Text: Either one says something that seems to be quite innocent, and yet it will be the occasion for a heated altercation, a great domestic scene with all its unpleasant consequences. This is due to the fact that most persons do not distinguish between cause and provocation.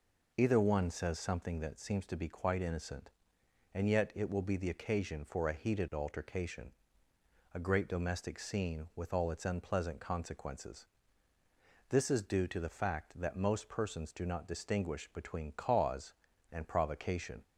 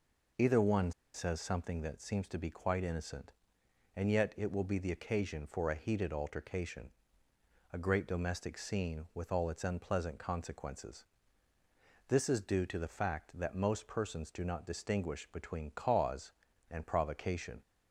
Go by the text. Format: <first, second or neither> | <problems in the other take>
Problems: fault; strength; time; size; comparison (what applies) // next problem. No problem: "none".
first | pauses between "one" and "says"; slight; at 0.9 s; 0.23 s long